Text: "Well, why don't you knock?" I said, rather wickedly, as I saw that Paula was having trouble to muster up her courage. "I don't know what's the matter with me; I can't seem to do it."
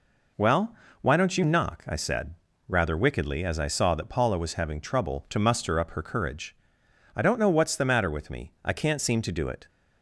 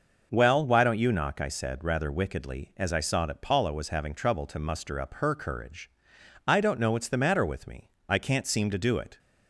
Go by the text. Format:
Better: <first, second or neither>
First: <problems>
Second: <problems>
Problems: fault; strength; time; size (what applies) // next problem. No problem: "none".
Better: neither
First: none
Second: none